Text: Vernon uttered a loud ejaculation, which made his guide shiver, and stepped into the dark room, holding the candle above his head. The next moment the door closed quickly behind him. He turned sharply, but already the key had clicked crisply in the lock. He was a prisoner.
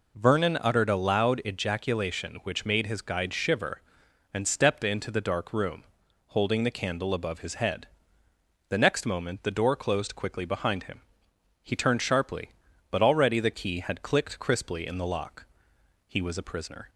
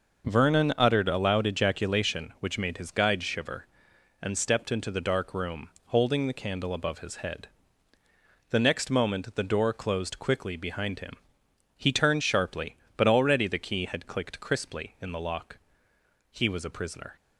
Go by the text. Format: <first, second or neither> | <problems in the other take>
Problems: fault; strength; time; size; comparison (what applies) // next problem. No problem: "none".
neither | none